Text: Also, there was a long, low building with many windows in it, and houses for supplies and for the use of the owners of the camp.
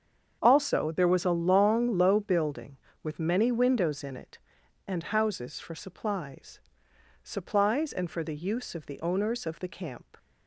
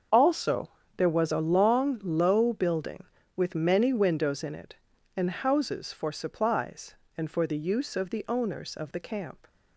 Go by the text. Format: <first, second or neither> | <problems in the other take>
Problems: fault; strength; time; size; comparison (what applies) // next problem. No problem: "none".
second | starts louder than the rest; strong; until 1.4 s; 7.5 dB; also in the second // says "supplies" twice; at 7.2 s